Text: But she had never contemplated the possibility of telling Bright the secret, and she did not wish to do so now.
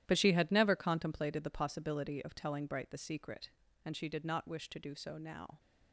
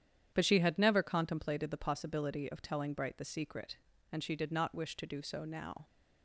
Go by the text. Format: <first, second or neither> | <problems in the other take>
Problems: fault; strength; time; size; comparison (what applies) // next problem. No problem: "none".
second | gets quieter; strong; throughout; 12.5 dB // starts louder than the rest; strong; until 1.0 s; 12 dB; strong in the second